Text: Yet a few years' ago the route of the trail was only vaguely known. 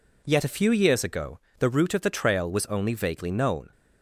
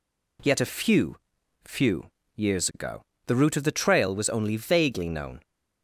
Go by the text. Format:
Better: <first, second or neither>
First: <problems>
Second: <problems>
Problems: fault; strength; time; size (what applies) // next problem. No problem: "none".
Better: first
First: pauses between "ago" and "the"; slight; at 1.3 s; 0.18 s long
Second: says "few" twice; at 1.6 s // pauses between "ago" and "the"; slight; at 3.0 s; 0.26 s long